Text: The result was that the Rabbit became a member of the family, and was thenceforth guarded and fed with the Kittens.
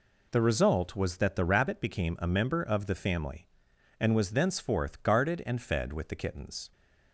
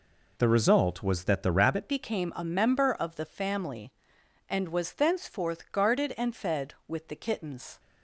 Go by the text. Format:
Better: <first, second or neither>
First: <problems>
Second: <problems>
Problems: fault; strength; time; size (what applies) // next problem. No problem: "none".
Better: first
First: none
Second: changes voice at "became"; from 1.8 s on; 5.9 s long